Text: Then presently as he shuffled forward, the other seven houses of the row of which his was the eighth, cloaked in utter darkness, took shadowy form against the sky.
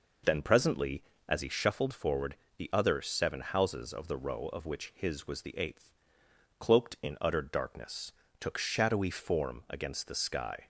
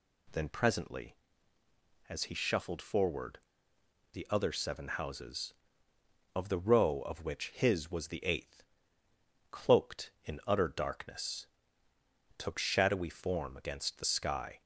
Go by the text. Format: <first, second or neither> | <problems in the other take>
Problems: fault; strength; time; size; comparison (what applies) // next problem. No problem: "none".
neither | none